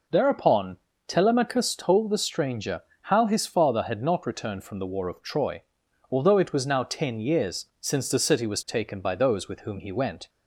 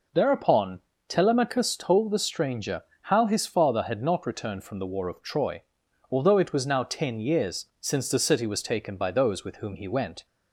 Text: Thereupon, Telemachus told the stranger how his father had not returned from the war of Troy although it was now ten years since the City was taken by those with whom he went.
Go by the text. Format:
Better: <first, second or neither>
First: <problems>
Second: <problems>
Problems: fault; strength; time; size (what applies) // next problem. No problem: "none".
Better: neither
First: pauses between "stranger" and "how"; slight; at 2.8 s; 0.22 s long // pauses between "Troy" and "although"; noticeable; at 5.6 s; 0.48 s long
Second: pauses between "stranger" and "how"; slight; at 2.8 s; 0.21 s long // pauses between "Troy" and "although"; noticeable; at 5.6 s; 0.48 s long